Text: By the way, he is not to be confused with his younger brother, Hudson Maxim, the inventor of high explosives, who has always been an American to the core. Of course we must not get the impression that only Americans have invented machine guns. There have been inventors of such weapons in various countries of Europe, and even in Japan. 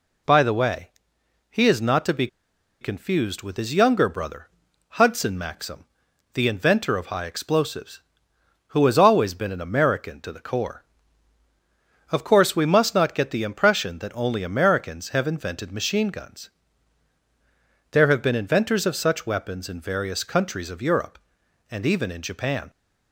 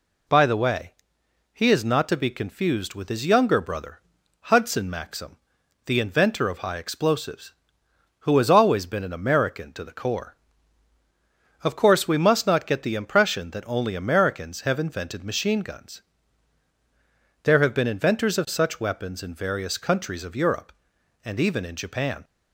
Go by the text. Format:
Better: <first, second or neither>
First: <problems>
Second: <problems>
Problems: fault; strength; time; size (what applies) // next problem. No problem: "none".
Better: second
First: pauses between "be" and "confused"; noticeable; at 2.2 s; 0.54 s long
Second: none